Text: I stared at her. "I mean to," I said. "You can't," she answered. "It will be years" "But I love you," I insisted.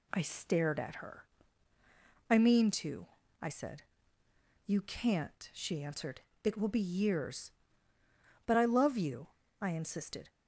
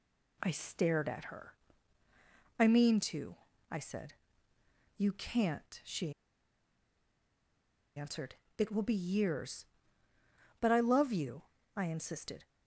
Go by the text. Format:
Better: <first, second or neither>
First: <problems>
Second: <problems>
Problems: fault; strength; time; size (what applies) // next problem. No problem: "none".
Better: first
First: none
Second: pauses between "she" and "answered"; strong; at 6.1 s; 1.8 s long